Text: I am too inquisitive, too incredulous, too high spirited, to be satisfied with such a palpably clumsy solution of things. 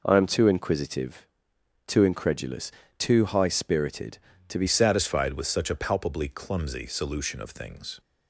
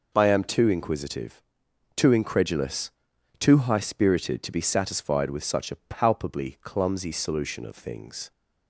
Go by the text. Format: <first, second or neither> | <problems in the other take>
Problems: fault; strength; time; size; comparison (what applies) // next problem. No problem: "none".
second | changes voice at "satisfied"; from 4.6 s on; 3.3 s long